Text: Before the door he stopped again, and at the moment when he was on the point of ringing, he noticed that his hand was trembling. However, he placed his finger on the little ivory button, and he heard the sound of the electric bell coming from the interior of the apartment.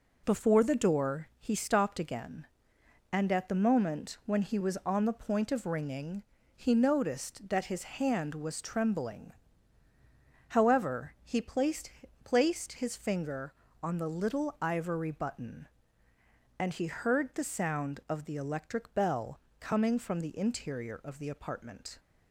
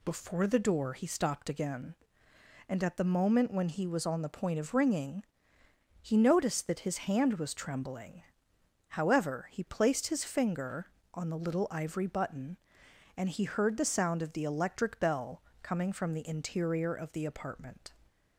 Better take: second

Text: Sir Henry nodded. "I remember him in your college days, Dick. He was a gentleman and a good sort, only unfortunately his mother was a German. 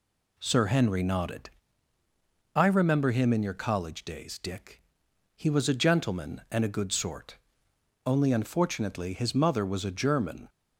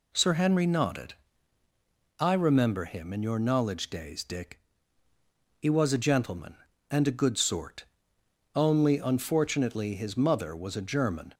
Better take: first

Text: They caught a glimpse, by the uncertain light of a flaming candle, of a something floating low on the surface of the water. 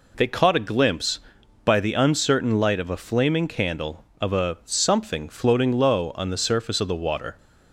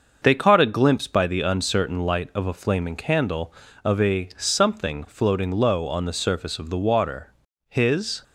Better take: first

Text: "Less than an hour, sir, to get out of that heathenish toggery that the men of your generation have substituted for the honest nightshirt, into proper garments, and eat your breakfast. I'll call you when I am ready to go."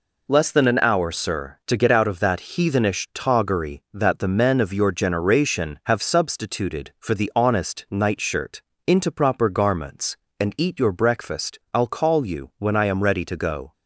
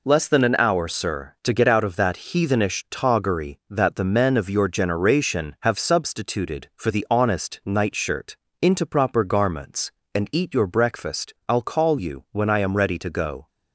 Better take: neither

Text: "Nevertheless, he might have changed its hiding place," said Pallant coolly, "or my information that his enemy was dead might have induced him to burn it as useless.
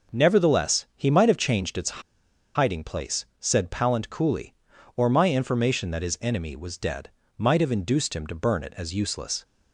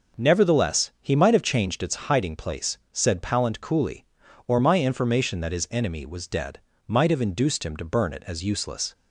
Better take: second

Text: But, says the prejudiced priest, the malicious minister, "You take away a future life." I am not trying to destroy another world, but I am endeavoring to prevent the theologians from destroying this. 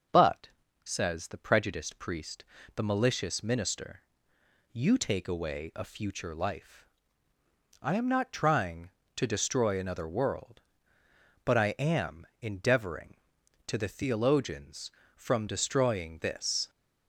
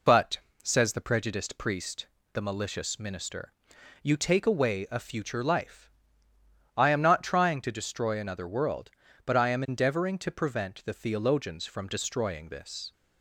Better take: second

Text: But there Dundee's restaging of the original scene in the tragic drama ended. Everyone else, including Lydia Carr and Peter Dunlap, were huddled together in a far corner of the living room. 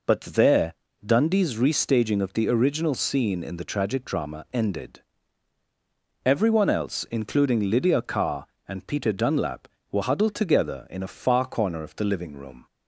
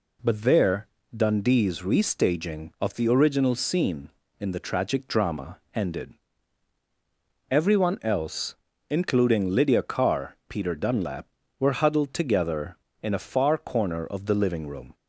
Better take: first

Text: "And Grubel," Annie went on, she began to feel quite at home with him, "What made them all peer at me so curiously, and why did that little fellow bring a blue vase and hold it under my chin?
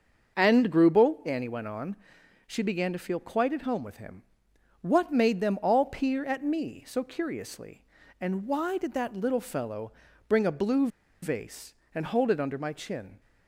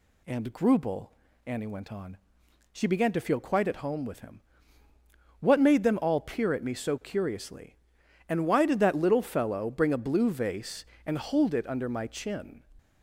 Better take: second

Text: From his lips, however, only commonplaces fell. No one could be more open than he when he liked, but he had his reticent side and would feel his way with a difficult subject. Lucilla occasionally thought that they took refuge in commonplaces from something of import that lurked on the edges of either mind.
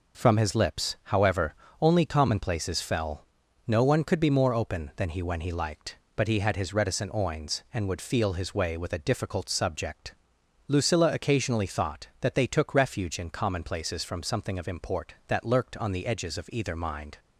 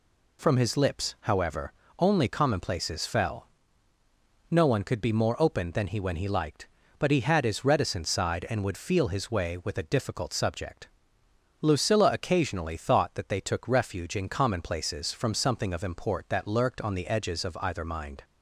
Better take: second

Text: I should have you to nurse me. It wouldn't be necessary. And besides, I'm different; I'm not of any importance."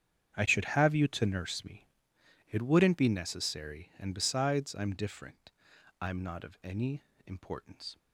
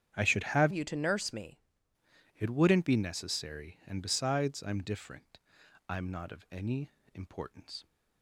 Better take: first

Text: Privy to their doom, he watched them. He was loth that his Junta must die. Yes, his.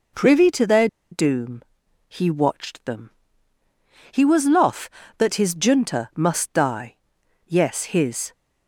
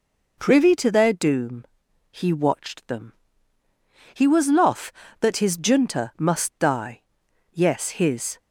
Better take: second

